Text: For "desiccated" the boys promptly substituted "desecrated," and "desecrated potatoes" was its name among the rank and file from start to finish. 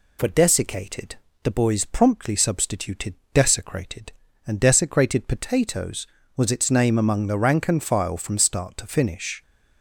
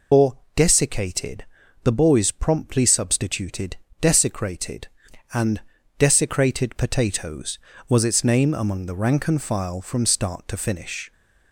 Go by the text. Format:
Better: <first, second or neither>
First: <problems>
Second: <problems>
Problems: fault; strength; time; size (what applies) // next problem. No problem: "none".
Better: first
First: pauses between "desiccated" and "the"; slight; at 1.1 s; 0.28 s long // pauses between "substituted" and "desecrated"; slight; at 3.1 s; 0.18 s long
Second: loses the start of "For"; at 0.1 s; 135 ms // pauses between "For" and "desiccated"; slight; at 0.3 s; 0.18 s long // pauses between "desiccated" and "the"; at 1.4 s; 0.38 s long // pauses between "substituted" and "desecrated"; slight; at 3.7 s; 0.26 s long // pauses between "and" and "desecrated"; slight; at 5.6 s; 0.36 s long